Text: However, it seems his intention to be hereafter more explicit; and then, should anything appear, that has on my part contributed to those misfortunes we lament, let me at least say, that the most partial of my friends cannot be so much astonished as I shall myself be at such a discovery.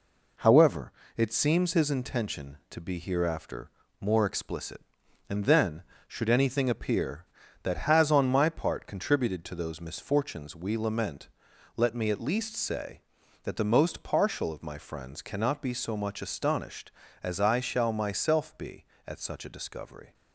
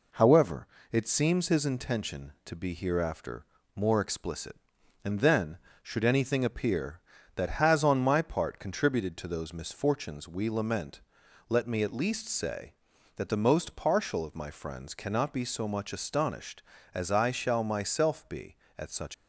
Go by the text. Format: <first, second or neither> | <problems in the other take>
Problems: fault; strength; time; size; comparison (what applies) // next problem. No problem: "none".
first | pauses between "hereafter" and "more"; slight; at 3.4 s; 0.28 s long; slight in the first // stops before "a discovery"; at 19.1 s